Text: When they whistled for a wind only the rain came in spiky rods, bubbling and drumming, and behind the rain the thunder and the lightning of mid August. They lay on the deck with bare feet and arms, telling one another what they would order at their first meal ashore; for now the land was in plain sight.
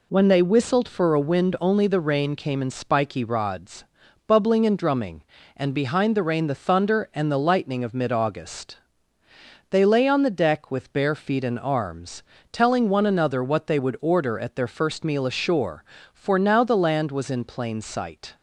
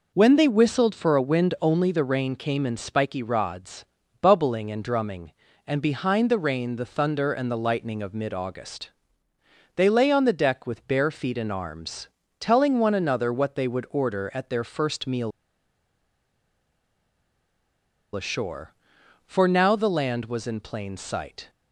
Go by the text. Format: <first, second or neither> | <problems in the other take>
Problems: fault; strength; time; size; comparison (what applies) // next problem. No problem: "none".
first | pauses between "meal" and "ashore"; strong; at 15.3 s; 2.8 s long